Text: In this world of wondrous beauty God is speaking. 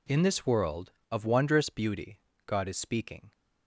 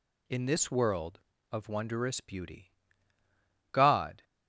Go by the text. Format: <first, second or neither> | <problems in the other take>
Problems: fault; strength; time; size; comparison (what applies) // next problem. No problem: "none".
first | pauses between "beauty" and "God"; at 2.7 s; 1.0 s long; slight in the first // stops before "is speaking"; at 4.2 s